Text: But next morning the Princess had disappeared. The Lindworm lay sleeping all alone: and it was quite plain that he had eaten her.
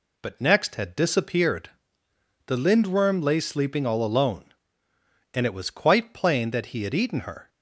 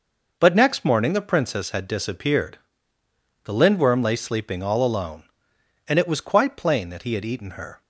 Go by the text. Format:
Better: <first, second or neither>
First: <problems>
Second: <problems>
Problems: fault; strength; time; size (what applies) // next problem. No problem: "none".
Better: second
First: skips "morning the Princess"; at 0.7 s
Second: none